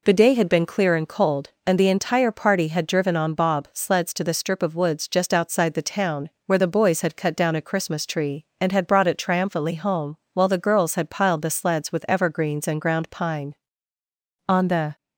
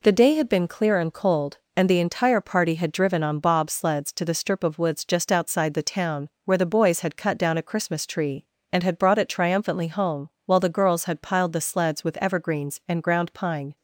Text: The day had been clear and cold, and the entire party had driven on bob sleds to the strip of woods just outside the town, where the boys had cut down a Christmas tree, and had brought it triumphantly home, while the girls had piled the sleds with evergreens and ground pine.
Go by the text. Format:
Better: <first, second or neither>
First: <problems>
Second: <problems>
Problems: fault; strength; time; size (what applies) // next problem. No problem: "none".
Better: second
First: goes on to say "On the"; slight; from 14.4 s on; 0.48 s long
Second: none